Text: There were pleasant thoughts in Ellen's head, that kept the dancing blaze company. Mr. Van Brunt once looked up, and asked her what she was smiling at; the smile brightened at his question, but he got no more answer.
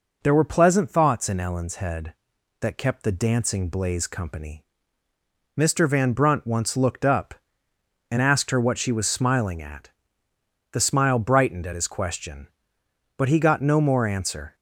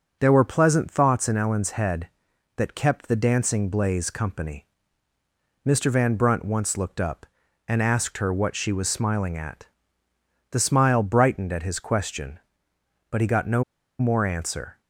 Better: first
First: none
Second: pauses between "no" and "more"; at 13.6 s; 0.36 s long

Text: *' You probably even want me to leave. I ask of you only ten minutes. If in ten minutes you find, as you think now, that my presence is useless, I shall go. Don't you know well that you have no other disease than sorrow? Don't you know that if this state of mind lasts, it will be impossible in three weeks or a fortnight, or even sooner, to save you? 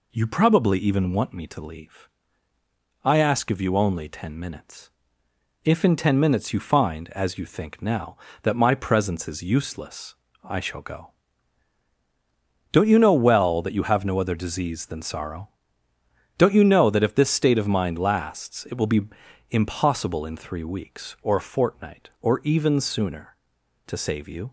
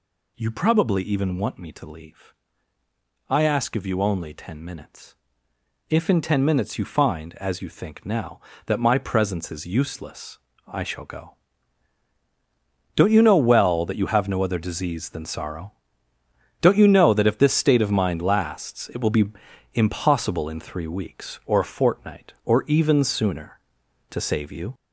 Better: first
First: pauses between "be" and "impossible"; noticeable; at 19.0 s; 0.48 s long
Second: gets louder; noticeable; throughout; 4.5 dB // pauses between "be" and "impossible"; noticeable; at 19.2 s; 0.48 s long

